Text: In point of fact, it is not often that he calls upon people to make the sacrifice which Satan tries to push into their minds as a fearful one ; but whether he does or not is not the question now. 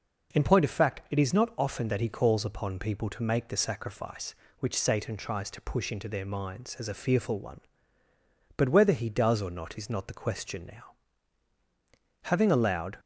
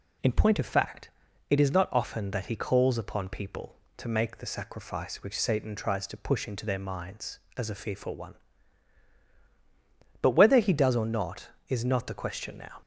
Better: second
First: goes on to say "Having allowed"; noticeable; from 12.2 s on; 0.78 s long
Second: none

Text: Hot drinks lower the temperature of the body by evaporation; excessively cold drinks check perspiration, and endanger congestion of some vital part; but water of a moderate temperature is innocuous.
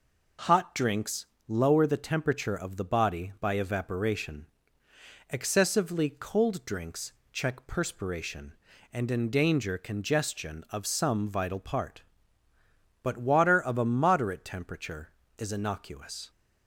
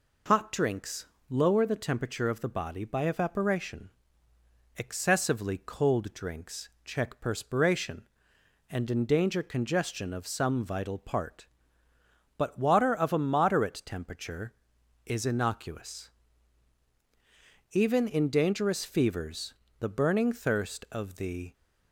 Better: first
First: pauses between "drinks" and "lower"; slight; at 1.2 s; 0.24 s long // pauses between "drinks" and "check"; slight; at 7.1 s; 0.22 s long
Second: pauses between "drinks" and "lower"; slight; at 1.0 s; 0.22 s long // pauses between "drinks" and "check"; slight; at 6.6 s; 0.16 s long // goes on to say "Even in dangerous fevers the burning thirst of the"; strong; from 17.7 s on; 3.8 s long

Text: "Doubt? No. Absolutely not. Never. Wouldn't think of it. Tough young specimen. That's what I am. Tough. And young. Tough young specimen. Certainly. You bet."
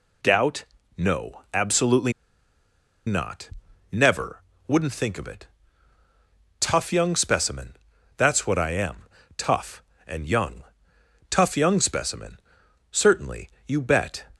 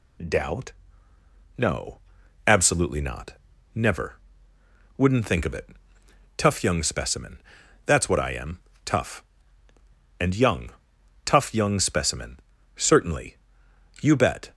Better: second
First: pauses between "Absolutely" and "not"; noticeable; at 2.1 s; 0.94 s long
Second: none

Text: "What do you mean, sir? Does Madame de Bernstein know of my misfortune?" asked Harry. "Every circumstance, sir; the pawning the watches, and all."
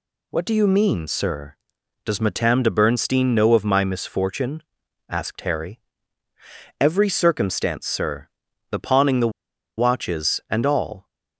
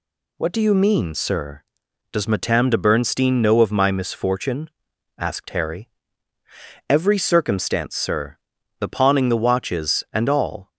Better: second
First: pauses between "the" and "watches"; noticeable; at 9.3 s; 0.48 s long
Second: none

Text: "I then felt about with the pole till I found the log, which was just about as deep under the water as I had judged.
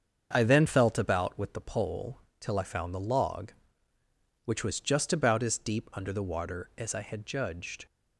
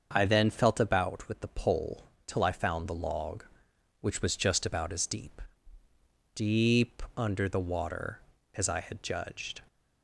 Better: first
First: starts louder than the rest; strong; until 1.3 s; 7 dB // pauses between "pole" and "till"; slight; at 2.2 s; 0.18 s long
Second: starts louder than the rest; until 1.1 s; 7 dB // pauses between "pole" and "till"; slight; at 2.0 s; 0.20 s long // says "deep" twice; at 6.3 s

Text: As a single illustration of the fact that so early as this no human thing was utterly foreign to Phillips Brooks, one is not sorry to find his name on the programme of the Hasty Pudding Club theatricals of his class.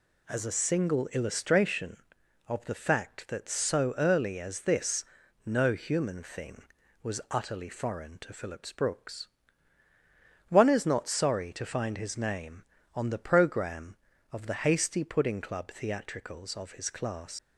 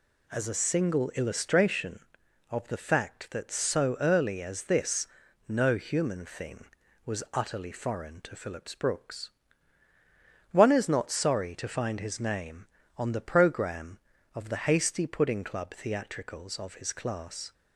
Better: second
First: pauses between "this" and "no"; at 5.0 s; 0.40 s long // leaves "class" unfinished; at 17.3 s; 115 ms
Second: pauses between "this" and "no"; at 5.0 s; 0.40 s long

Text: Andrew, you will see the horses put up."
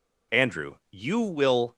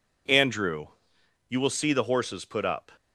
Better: second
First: stops before "see the horses put up"; at 1.7 s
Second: none

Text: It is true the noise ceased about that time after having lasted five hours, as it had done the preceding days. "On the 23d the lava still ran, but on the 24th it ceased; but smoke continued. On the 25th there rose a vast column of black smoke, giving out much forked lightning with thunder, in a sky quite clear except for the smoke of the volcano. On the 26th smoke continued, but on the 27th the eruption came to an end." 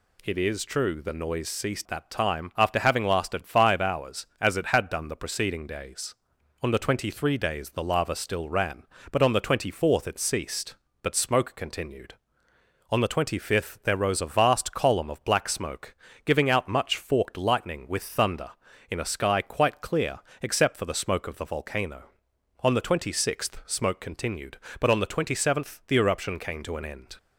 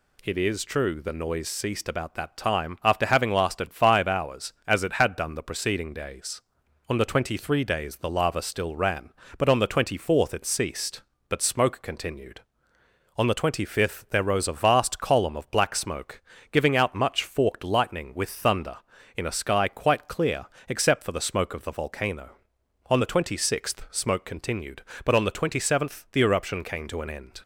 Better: second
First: skips "about"; at 1.8 s // pauses between "clear" and "except"; slight; at 20.1 s; 0.22 s long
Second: pauses between "clear" and "except"; slight; at 20.4 s; 0.22 s long

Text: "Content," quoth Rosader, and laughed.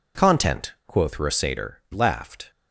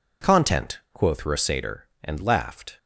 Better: second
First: skips "and"; at 1.8 s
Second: none

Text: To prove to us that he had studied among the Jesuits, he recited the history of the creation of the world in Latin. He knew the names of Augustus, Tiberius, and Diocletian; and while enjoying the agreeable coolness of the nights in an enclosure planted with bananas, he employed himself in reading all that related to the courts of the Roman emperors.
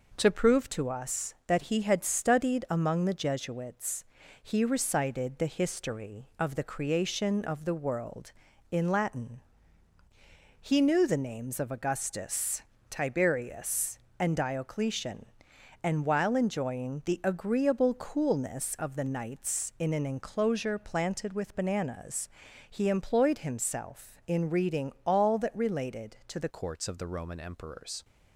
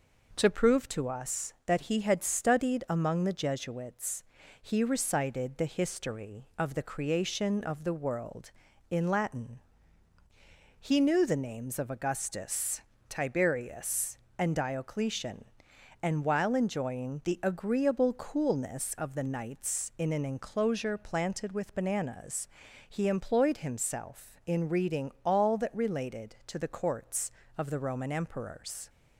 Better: second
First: changes voice at "courts"; from 26.4 s on; 1.6 s long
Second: none

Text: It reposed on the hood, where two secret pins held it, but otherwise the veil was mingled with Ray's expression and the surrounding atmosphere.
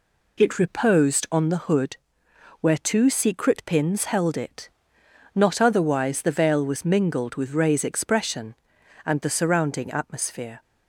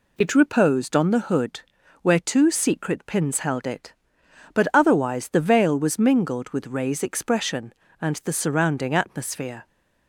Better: second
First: says "not" for "but"; at 5.3 s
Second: none

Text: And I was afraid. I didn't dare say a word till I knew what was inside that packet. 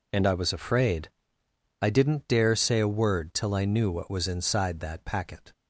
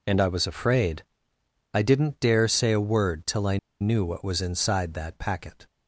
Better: first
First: none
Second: pauses between "I" and "knew"; slight; at 3.5 s; 0.24 s long

